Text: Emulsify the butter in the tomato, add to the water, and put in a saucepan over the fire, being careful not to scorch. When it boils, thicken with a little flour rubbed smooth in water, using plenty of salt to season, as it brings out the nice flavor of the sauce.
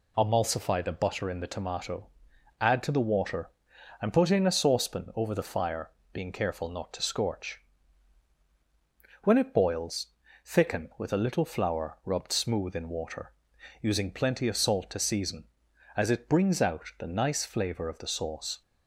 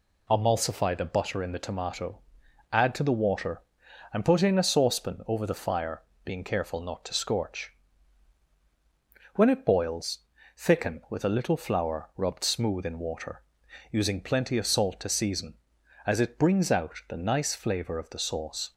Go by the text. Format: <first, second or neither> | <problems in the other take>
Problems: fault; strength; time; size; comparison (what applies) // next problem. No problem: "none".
neither | none